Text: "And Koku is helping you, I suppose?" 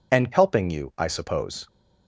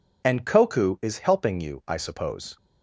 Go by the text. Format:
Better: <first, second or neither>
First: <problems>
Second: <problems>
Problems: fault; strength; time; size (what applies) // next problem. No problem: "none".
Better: second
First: skips "Koku is"; at 0.3 s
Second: none